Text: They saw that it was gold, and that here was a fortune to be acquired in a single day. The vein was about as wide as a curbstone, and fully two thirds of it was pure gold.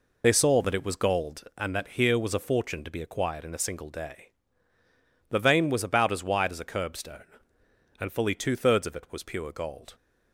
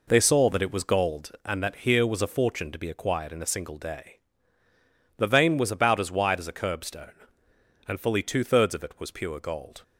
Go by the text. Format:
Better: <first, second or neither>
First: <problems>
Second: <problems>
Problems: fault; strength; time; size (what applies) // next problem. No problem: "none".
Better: second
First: loses the start of "They"; at 0.2 s; 50 ms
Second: none